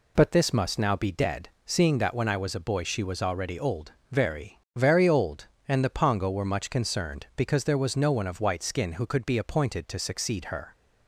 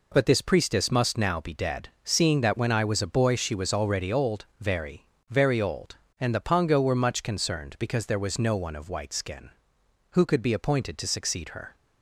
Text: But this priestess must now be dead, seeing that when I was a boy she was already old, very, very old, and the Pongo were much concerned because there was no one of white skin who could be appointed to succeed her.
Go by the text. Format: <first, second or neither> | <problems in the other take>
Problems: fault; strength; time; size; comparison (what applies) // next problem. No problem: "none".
second | skips "priestess"; at 0.5 s